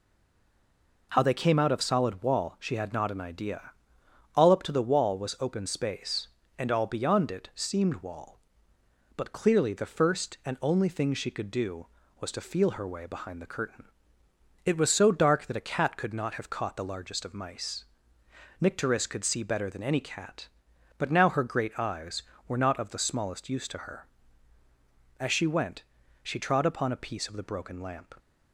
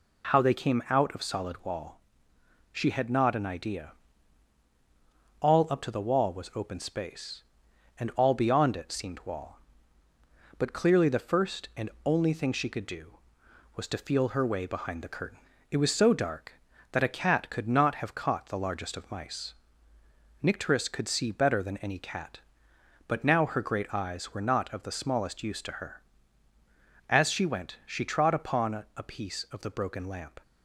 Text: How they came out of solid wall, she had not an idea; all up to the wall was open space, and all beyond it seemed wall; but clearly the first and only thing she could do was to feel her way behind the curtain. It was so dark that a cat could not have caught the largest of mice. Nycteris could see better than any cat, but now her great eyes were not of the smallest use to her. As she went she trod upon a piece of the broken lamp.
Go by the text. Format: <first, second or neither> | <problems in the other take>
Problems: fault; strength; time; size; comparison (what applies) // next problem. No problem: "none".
second | stays silent before the first word; until 1.1 s; 1.1 s long // pauses between "went" and "she"; at 25.8 s; 0.40 s long